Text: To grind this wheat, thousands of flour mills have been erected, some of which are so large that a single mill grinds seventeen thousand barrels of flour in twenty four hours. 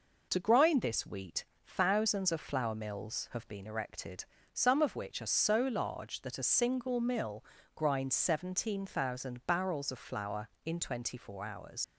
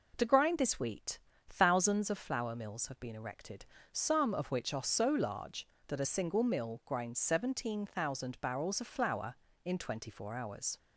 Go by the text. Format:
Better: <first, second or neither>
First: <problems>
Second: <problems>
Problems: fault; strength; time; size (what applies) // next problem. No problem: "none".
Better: second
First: pauses between "mill" and "grinds"; slight; at 7.4 s; 0.32 s long // leaves "hours" unfinished; at 11.8 s; 90 ms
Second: none